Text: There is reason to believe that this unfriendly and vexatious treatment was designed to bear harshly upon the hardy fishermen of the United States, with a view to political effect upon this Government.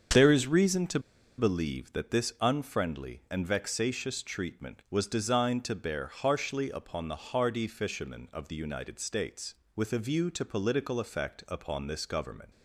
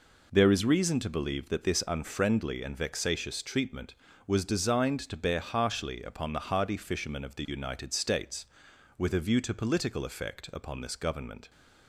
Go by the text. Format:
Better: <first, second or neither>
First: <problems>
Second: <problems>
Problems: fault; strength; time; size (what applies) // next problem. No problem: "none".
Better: second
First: starts louder than the rest; strong; until 1.5 s; 7 dB // pauses between "to" and "believe"; at 0.9 s; 0.38 s long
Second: none